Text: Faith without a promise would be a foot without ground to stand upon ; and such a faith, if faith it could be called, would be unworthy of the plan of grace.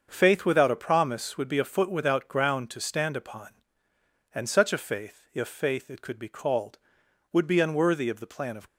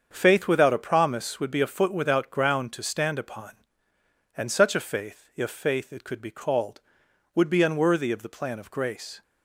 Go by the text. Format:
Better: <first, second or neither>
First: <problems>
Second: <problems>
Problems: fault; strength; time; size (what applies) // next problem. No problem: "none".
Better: second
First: starts louder than the rest; until 1.1 s; 6.5 dB // stops before "grace"; at 8.6 s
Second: starts louder than the rest; until 1.1 s; 7 dB